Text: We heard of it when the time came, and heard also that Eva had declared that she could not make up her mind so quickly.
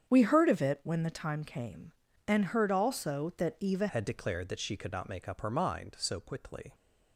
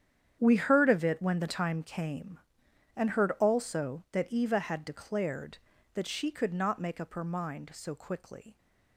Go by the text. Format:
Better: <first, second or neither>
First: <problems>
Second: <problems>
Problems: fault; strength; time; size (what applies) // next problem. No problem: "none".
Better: second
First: starts louder than the rest; strong; until 1.1 s; 8 dB // changes voice at "had"; from 3.8 s on; 2.9 s long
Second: starts louder than the rest; strong; until 1.4 s; 9 dB